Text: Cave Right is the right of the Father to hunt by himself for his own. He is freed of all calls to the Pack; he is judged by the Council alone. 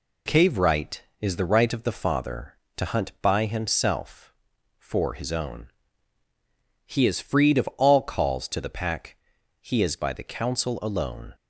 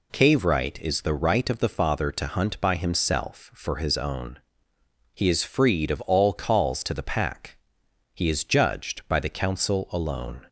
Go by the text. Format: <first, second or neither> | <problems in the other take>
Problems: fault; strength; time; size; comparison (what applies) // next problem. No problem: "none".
second | skips "judged"; at 9.9 s